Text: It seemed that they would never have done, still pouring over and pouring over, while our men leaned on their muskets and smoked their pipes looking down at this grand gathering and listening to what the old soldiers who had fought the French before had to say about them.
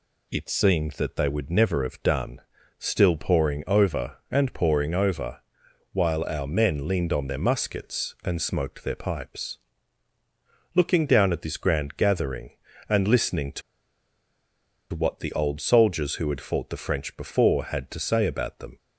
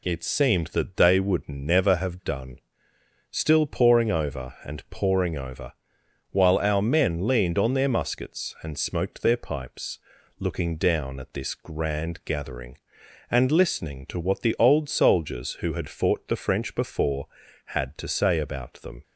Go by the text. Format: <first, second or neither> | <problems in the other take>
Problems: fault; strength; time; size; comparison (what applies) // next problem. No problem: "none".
second | pauses between "pipes" and "looking"; at 9.5 s; 1.1 s long; also in the second // pauses between "to" and "what"; strong; at 13.6 s; 1.3 s long